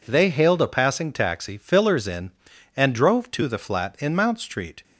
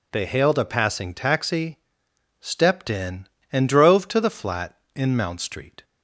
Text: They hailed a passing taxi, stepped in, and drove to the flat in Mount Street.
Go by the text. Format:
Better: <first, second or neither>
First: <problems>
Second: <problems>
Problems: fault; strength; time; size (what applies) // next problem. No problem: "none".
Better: second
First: says "fillers" for "stepped"; at 1.5 s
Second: none